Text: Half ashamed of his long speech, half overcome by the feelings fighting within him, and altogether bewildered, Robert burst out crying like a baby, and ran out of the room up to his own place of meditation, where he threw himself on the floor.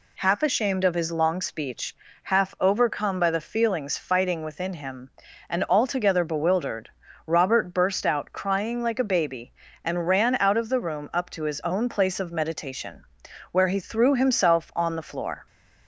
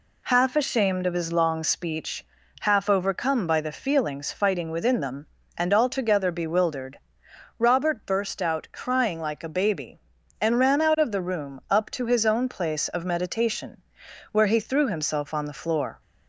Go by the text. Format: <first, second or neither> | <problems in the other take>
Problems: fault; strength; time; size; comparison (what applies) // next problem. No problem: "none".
first | says "them" for "him"; at 5.0 s